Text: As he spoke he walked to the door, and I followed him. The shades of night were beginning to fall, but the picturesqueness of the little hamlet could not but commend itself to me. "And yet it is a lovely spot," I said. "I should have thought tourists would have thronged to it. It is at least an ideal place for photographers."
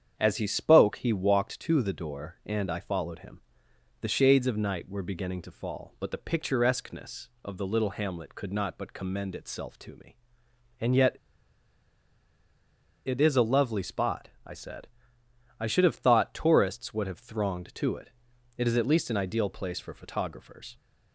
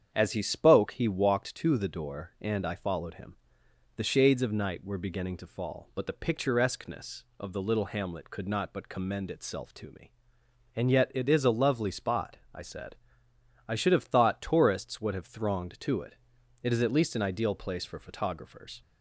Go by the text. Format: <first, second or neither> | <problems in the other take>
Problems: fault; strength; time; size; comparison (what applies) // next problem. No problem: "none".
second | starts louder than the rest; strong; until 1.1 s; 8 dB; strong in the second // pauses between "yet" and "it"; strong; at 11.1 s; 1.9 s long